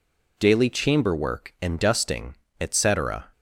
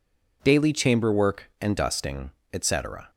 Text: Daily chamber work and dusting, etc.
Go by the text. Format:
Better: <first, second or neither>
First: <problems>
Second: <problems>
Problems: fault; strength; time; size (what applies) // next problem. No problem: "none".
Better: neither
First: none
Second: none